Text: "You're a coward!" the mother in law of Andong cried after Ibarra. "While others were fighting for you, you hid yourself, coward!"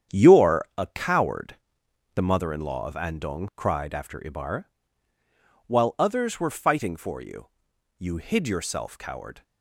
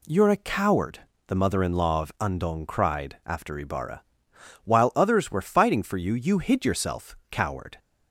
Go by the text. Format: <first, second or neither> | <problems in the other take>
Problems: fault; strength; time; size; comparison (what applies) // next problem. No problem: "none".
second | gets quieter; strong; throughout; 8 dB